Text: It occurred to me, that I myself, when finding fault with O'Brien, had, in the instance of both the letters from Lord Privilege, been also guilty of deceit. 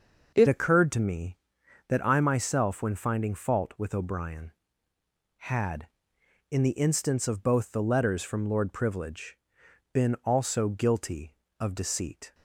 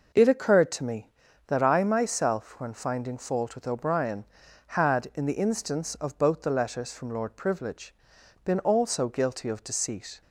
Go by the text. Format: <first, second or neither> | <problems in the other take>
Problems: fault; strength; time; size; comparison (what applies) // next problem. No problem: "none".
second | changes voice at "occurred"; from 0.4 s on; 11.9 s long